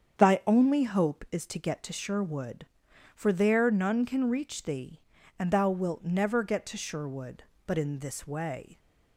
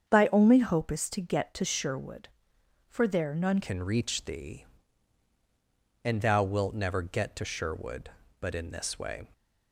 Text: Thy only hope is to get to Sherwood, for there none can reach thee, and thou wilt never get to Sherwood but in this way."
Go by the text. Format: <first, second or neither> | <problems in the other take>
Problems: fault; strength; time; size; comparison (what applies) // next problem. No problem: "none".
first | starts louder than the rest; strong; until 1.1 s; 7.5 dB; strong in the first // changes voice at "can"; from 3.6 s on; 5.6 s long